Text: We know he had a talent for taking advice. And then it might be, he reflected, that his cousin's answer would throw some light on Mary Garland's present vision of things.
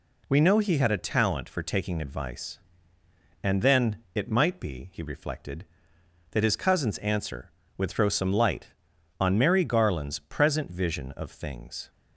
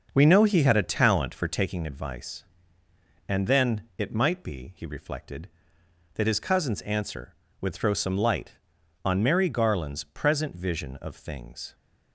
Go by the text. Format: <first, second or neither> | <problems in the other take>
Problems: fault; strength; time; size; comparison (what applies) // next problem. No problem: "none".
first | starts louder than the rest; until 1.8 s; 6 dB // pauses between "then" and "it"; slight; at 3.8 s; 0.16 s long; slight in the first